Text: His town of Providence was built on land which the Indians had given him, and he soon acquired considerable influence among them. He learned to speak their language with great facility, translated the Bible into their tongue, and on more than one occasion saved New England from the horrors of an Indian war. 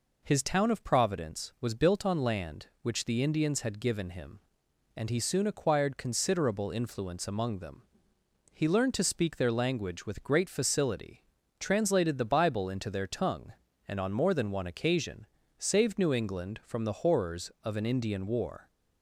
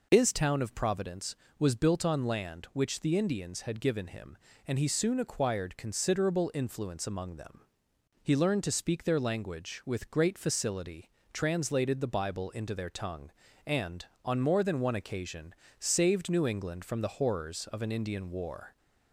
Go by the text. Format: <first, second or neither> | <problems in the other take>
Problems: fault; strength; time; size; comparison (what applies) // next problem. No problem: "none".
neither | pauses between "occasion" and "saved"; slight; the same in both